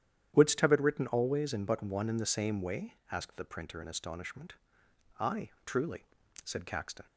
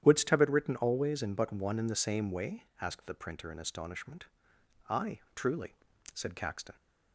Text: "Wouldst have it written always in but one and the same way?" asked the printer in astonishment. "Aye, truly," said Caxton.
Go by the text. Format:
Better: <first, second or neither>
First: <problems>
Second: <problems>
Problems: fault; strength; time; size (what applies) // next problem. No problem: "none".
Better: neither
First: starts louder than the rest; strong; until 1.3 s; 10 dB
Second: starts louder than the rest; strong; until 1.0 s; 10 dB